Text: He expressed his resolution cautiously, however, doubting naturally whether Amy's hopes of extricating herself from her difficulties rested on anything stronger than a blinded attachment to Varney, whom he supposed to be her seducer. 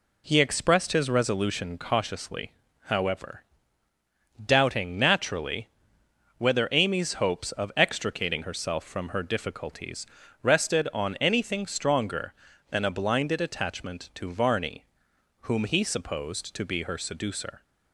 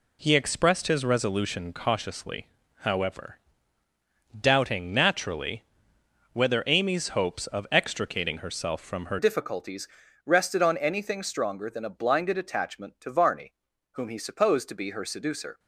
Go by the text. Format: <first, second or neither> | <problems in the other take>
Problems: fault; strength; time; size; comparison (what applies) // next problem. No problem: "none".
first | pauses between "naturally" and "whether"; noticeable; at 5.6 s; 0.72 s long; noticeable in the first // changes voice at "difficulties"; from 9.1 s on; 6.4 s long // pauses between "difficulties" and "rested"; slight; at 9.8 s; 0.36 s long; slight in the first